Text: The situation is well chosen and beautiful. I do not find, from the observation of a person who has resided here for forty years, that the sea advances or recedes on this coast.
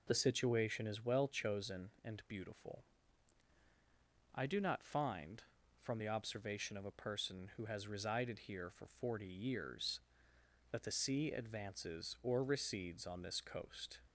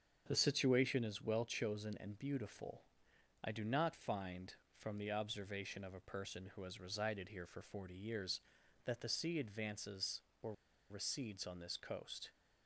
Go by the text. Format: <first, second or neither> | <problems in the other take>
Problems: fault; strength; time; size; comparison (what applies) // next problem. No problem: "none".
first | starts louder than the rest; strong; until 1.2 s; 7 dB // pauses between "or" and "recedes"; at 10.5 s; 0.37 s long